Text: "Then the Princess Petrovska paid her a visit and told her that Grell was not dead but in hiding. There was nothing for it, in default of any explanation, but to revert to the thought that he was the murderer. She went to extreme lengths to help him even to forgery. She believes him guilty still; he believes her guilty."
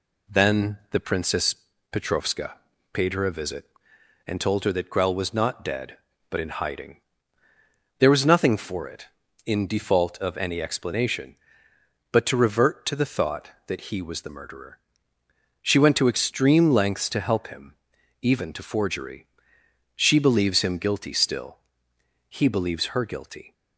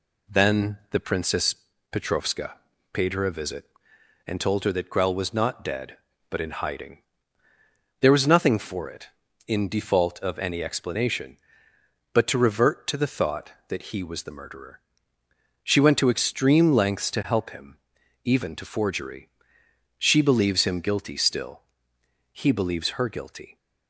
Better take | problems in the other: neither | pauses between "Princess" and "Petrovska"; slight; the same in both // pauses between "Petrovska" and "paid"; slight; the same in both // pauses between "him" and "even"; noticeable; the same in both

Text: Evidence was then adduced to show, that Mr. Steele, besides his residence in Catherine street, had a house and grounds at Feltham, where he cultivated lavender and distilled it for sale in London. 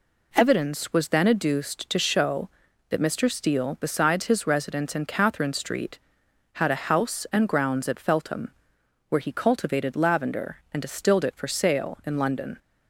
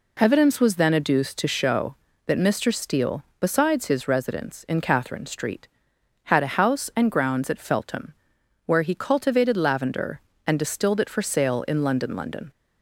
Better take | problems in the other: first | says "London" twice; at 12.1 s

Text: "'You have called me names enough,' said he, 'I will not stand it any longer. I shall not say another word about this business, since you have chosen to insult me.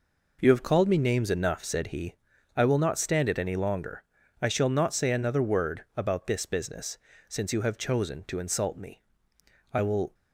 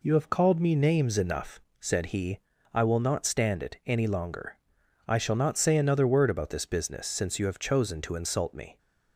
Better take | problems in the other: second | goes on to say "I will"; slight; from 9.7 s on; 0.40 s long

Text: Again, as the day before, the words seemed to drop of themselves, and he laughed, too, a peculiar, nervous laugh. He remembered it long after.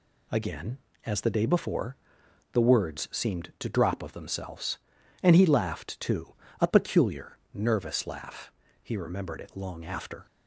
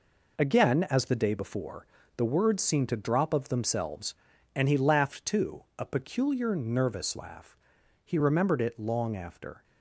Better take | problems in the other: first | gets quieter; strong; throughout; 7.5 dB

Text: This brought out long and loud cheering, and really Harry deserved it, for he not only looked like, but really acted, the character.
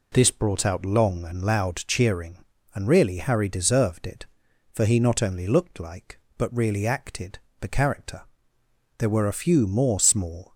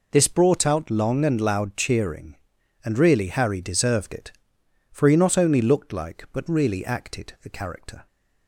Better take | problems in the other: second | goes on to say "There were a few more small"; from 8.9 s on; 1.5 s long

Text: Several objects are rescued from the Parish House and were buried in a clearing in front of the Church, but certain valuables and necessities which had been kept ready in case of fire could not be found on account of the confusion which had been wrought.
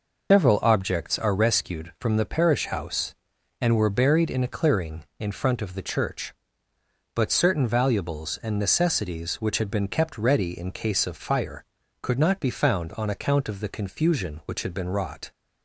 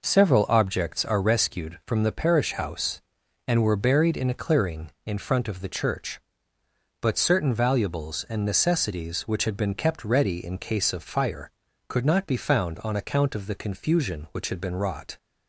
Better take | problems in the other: second | loses the start of "Several"; at 0.3 s; 135 ms

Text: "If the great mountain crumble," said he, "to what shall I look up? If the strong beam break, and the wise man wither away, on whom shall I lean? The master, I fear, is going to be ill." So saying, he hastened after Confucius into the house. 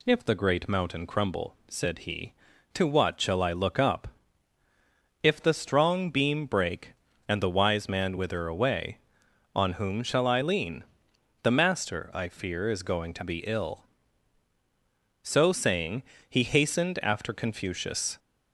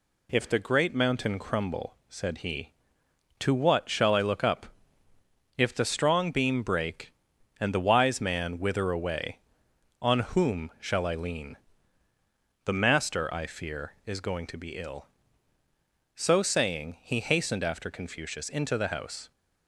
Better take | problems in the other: second | stops before "into the house"; at 18.1 s

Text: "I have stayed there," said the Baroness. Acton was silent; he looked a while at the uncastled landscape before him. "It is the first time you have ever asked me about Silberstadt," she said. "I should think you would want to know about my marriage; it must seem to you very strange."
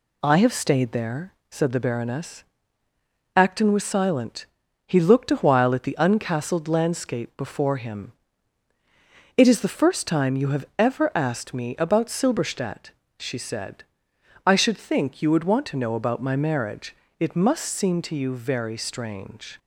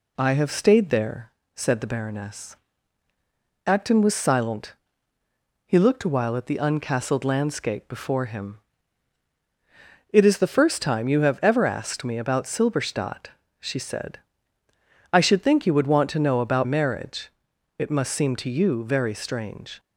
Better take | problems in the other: first | skips "my"; at 16.6 s

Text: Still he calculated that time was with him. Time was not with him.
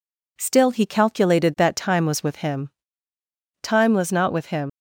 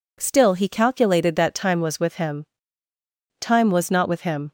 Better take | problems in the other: second | leaves "him" unfinished; at 4.6 s; 85 ms

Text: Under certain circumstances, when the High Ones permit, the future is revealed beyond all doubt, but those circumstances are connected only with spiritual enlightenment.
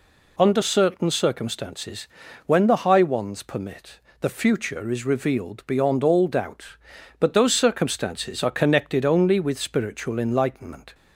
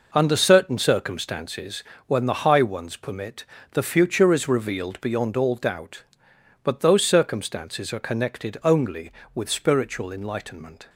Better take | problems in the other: first | gets quieter; strong; throughout; 8.5 dB

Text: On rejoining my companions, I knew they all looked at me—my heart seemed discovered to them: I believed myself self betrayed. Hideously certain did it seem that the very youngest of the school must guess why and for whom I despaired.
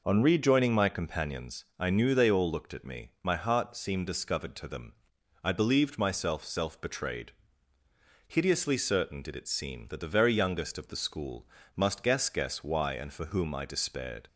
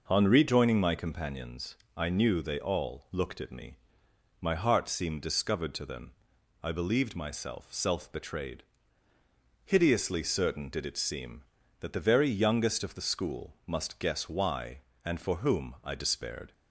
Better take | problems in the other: second | pauses between "school" and "must"; slight; at 11.4 s; 0.30 s long // says "guess" twice; at 12.2 s

